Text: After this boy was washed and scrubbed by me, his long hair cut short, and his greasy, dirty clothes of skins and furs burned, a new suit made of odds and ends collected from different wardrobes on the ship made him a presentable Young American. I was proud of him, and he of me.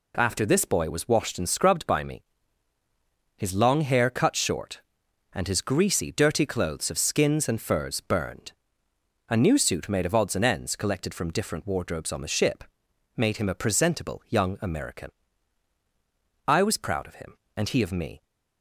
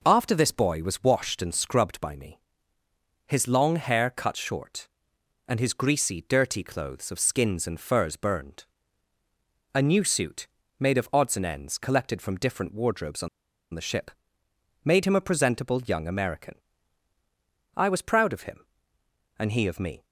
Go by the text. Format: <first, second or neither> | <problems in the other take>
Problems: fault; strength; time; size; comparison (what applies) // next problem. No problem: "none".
first | pauses between "suit" and "made"; slight; at 10.4 s; 0.32 s long // pauses between "on" and "the"; at 13.2 s; 0.45 s long // pauses between "ship" and "made"; noticeable; at 14.1 s; 0.72 s long; noticeable in the first